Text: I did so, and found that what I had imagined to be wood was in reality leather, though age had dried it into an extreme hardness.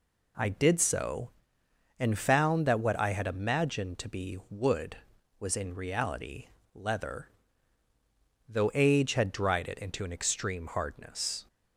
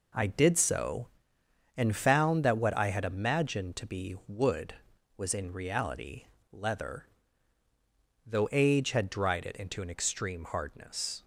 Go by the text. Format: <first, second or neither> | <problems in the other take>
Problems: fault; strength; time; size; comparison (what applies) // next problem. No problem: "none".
first | gets quieter; strong; throughout; 7.5 dB // pauses between "reality" and "leather"; slight; at 6.2 s; 0.26 s long; slight in the first